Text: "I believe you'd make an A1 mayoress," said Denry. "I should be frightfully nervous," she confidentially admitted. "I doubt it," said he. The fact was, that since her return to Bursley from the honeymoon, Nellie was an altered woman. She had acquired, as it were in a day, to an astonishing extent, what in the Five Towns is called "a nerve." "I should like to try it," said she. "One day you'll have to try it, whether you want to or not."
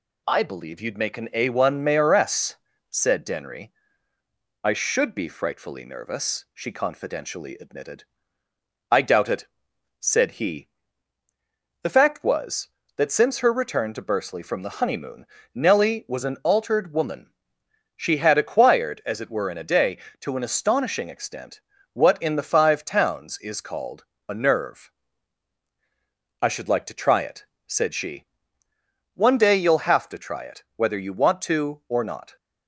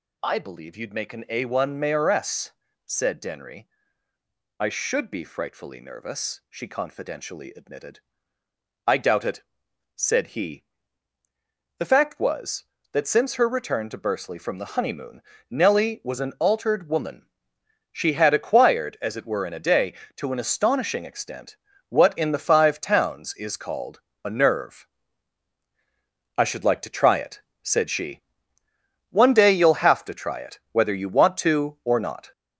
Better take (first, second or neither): first